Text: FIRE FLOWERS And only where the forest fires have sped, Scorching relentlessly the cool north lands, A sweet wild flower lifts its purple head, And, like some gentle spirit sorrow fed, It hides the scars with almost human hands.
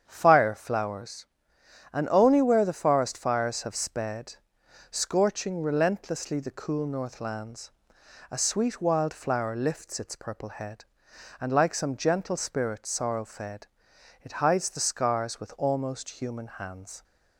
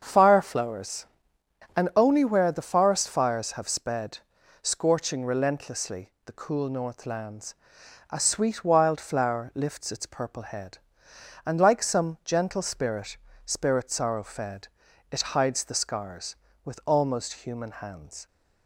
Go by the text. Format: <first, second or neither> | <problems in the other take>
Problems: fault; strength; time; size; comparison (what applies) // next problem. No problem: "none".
first | starts louder than the rest; until 1.0 s; 7 dB; strong in the first // says "spirit" twice; at 13.4 s